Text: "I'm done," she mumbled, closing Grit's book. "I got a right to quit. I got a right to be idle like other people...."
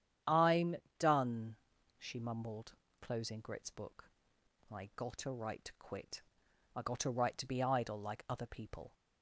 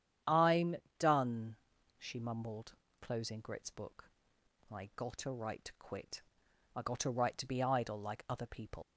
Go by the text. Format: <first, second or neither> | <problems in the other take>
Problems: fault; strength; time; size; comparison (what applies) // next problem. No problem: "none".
first | starts louder than the rest; strong; until 1.4 s; 9.5 dB; strong in the first // pauses between "I'm" and "done"; slight; at 0.7 s; 0.22 s long; slight in the first // leaves "people" unfinished; at 8.8 s; 105 ms